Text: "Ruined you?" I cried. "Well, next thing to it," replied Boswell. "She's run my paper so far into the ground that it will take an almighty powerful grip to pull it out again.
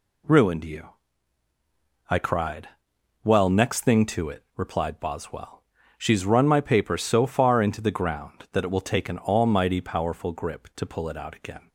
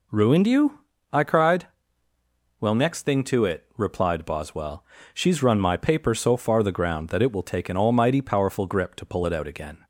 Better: first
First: none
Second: skips "into"; at 6.6 s

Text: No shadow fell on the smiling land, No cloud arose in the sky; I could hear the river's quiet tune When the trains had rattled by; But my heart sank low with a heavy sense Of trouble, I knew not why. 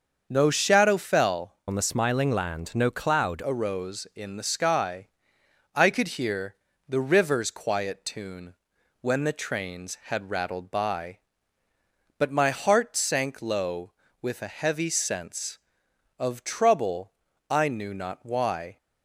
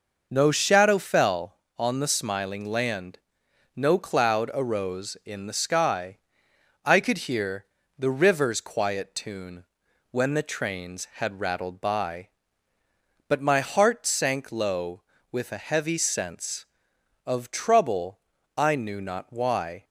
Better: second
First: starts louder than the rest; until 1.3 s; 6.5 dB // changes voice from "on" to "cloud"; from 1.6 to 3.4 s; 1.8 s long // pauses between "hear" and "the"; slight; at 6.5 s; 0.32 s long // pauses between "tune" and "When"; noticeable; at 8.5 s; 0.48 s long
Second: pauses between "hear" and "the"; slight; at 7.6 s; 0.32 s long // pauses between "tune" and "When"; noticeable; at 9.6 s; 0.48 s long

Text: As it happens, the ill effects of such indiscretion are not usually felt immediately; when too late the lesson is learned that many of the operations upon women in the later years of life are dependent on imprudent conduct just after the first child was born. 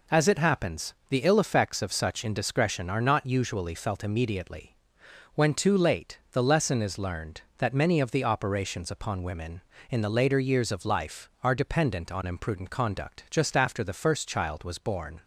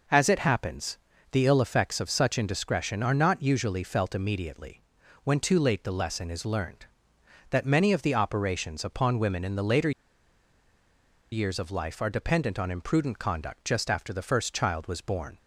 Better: first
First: none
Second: pauses between "later" and "years"; strong; at 9.9 s; 1.4 s long

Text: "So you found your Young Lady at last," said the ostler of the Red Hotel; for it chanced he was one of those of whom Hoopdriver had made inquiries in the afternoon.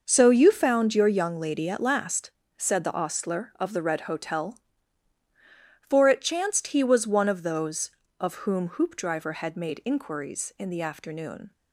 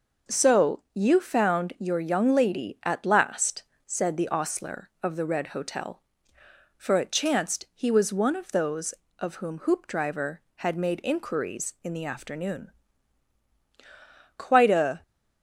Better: first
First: none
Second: goes on to say "Quite a"; noticeable; from 14.3 s on; 0.66 s long

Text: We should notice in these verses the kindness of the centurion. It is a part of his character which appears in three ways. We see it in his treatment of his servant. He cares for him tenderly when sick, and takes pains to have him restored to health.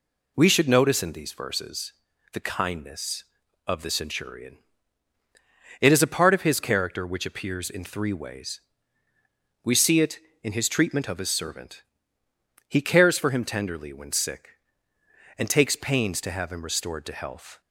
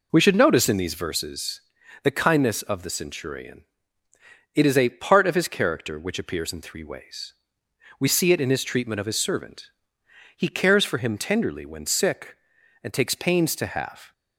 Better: first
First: pauses between "verses" and "the"; at 1.9 s; 0.40 s long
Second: pauses between "verses" and "the"; at 1.5 s; 0.42 s long // stops before "him restored to health"; at 14.1 s

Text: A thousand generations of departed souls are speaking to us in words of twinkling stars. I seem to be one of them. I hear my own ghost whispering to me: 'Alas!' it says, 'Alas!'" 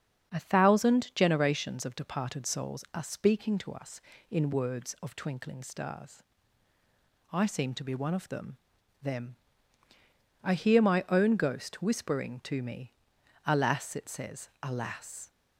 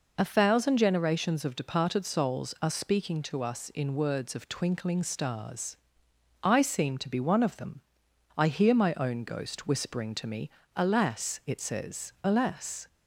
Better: second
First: starts louder than the rest; strong; until 1.3 s; 7.5 dB // says "them" twice; at 9.0 s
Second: none

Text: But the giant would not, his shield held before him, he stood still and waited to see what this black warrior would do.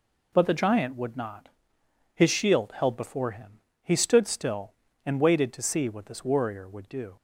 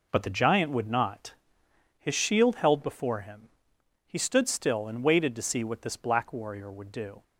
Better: second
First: skips "black"; at 6.2 s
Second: none

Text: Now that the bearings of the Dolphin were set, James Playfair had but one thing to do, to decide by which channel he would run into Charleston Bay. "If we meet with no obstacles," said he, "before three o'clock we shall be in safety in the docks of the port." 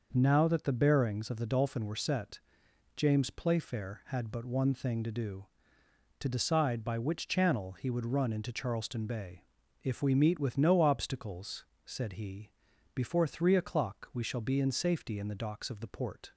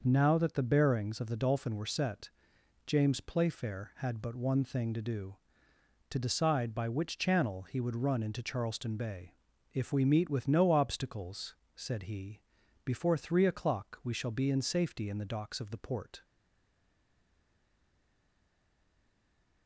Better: first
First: none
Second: stays silent after the last word; strong; from 16.2 s on; 3.4 s long

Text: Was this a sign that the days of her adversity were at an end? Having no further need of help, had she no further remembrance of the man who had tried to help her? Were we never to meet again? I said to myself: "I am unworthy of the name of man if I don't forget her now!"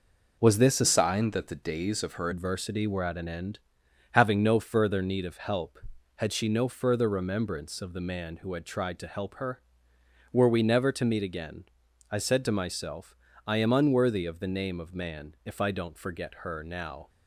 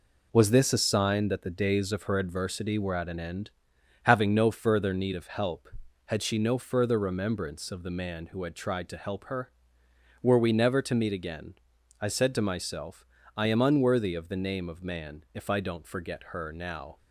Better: second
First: changes voice from "sign" to "her"; from 0.8 to 2.2 s; 1.4 s long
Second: none

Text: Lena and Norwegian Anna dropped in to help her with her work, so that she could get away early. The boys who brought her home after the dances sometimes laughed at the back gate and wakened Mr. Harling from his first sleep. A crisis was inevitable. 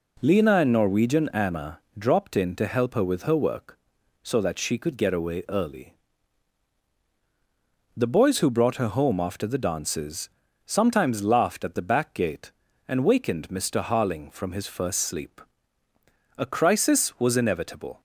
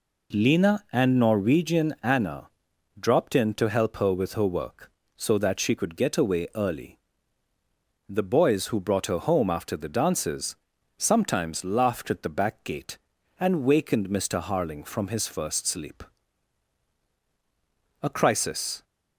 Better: first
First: pauses between "Anna" and "dropped"; slight; at 1.7 s; 0.18 s long // pauses between "dances" and "sometimes"; at 10.2 s; 0.38 s long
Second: pauses between "Anna" and "dropped"; noticeable; at 2.4 s; 0.50 s long // pauses between "dances" and "sometimes"; at 10.5 s; 0.42 s long // stops before "was inevitable"; at 18.8 s

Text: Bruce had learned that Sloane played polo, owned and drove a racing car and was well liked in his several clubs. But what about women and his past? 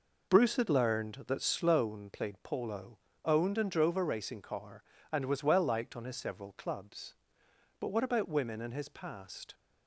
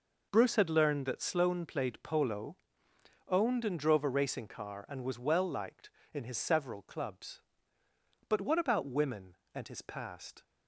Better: second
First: says "on" for "in"; at 5.9 s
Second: none

